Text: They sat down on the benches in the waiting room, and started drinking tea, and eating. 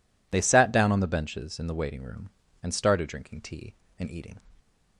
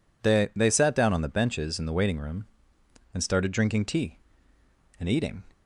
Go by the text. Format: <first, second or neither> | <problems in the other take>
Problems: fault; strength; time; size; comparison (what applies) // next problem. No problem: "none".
first | says "They" twice; at 0.5 s